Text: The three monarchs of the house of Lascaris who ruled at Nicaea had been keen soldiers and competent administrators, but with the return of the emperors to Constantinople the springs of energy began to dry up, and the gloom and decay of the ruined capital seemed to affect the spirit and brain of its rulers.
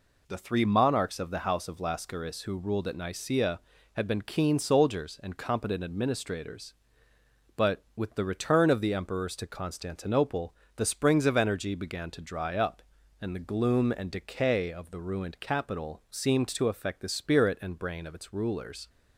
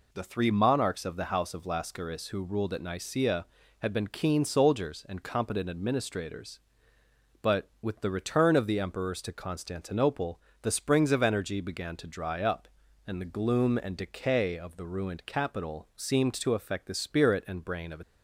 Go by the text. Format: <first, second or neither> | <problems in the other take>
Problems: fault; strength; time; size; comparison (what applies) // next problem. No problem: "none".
first | pauses between "Constantinople" and "the"; slight; at 10.4 s; 0.22 s long; slight in the first // stops before "its rulers"; at 18.0 s